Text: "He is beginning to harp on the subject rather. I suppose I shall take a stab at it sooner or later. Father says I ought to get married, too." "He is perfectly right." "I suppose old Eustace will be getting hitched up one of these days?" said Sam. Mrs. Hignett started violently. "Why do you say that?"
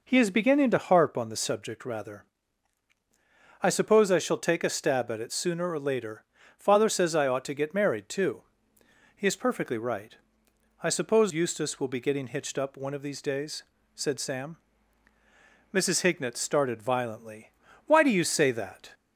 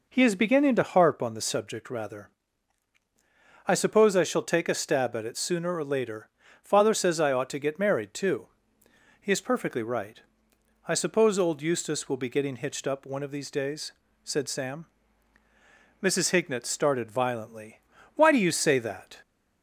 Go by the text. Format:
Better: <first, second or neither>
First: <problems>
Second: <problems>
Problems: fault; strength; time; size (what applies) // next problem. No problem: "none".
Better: second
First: skips "old"; at 11.3 s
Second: none